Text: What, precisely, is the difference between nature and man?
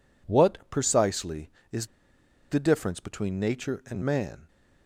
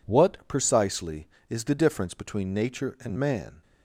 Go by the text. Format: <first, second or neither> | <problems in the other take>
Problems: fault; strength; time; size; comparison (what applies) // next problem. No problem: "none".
second | pauses between "is" and "the"; noticeable; at 1.8 s; 0.65 s long